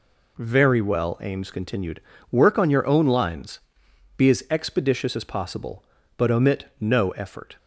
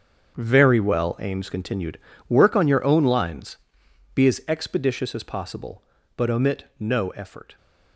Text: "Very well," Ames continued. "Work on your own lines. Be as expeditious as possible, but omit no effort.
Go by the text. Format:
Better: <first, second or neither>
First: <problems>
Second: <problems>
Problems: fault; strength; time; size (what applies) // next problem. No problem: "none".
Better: first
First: none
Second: gets quieter; strong; throughout; 12.5 dB